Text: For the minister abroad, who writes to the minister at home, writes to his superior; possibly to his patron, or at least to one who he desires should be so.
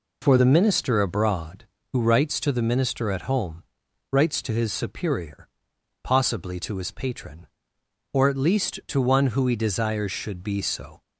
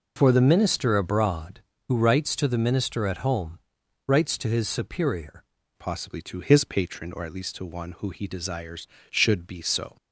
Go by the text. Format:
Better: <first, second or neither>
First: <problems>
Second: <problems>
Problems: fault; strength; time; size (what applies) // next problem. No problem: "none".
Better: first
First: none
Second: changes voice at "possibly"; from 5.7 s on; 4.2 s long